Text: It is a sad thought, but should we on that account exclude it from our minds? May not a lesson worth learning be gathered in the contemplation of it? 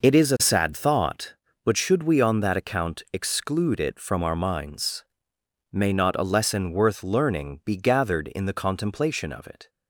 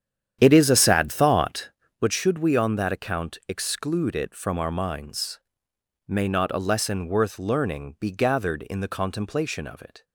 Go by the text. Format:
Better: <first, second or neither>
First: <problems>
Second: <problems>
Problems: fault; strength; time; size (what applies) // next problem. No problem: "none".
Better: first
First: none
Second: starts louder than the rest; strong; until 2.1 s; 9.5 dB